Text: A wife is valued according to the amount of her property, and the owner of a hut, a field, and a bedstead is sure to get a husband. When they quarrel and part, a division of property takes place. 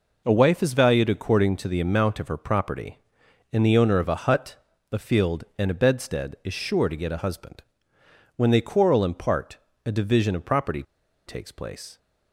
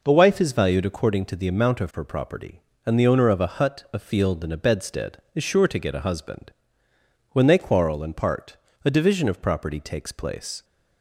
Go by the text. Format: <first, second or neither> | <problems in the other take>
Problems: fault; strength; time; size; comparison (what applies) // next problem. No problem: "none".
second | pauses between "property" and "takes"; at 10.8 s; 0.44 s long